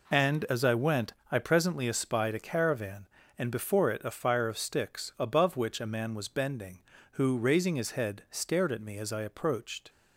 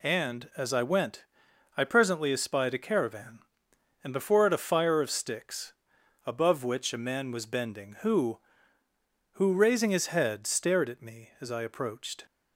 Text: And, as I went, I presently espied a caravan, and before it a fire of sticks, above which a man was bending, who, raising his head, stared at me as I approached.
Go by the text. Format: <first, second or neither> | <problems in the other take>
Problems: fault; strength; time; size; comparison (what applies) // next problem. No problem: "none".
first | says "who" twice; at 9.3 s